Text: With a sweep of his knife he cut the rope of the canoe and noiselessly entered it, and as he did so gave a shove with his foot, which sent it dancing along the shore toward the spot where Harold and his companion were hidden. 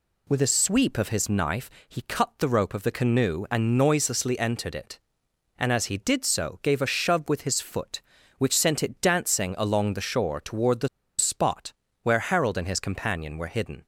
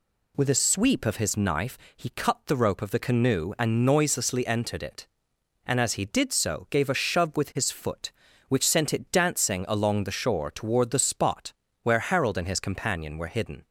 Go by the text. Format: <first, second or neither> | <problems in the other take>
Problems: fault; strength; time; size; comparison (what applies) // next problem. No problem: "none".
second | pauses between "knife" and "he"; slight; at 1.6 s; 0.18 s long; slight in the second // pauses between "the" and "spot"; slight; at 10.8 s; 0.30 s long // pauses between "spot" and "where"; slight; at 11.7 s; 0.30 s long; slight in the second